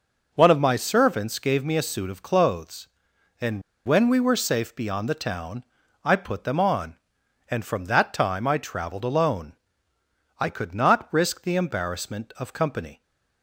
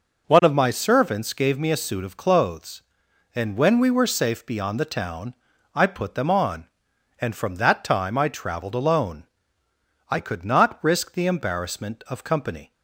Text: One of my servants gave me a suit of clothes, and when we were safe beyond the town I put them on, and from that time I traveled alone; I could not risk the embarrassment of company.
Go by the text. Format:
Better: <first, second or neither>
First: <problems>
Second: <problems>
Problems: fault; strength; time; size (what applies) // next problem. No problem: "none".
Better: second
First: pauses between "and" and "when"; slight; at 3.6 s; 0.25 s long // pauses between "town" and "I"; at 5.6 s; 0.38 s long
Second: pauses between "town" and "I"; at 5.3 s; 0.38 s long